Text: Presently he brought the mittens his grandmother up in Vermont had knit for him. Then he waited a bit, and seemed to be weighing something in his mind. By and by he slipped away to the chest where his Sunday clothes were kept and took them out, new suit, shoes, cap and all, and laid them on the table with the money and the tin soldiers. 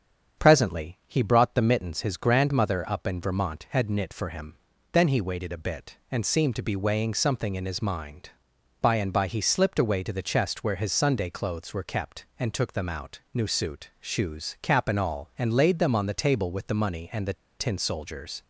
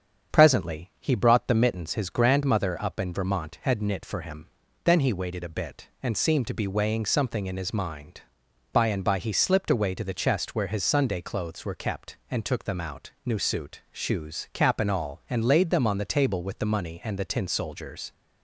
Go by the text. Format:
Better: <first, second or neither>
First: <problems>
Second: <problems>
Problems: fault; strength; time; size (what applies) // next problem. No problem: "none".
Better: second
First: starts louder than the rest; strong; until 1.4 s; 7.5 dB // pauses between "the" and "tin"; slight; at 17.3 s; 0.24 s long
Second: starts louder than the rest; strong; until 1.4 s; 7.5 dB